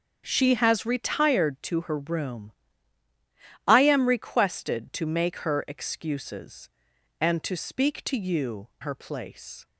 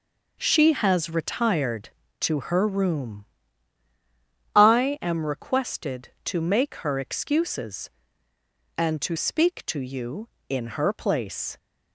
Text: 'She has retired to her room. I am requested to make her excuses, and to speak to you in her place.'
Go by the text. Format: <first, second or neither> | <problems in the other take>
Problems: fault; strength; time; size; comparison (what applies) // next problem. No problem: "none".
second | starts louder than the rest; strong; until 1.2 s; 7.5 dB // skips "in"; at 8.7 s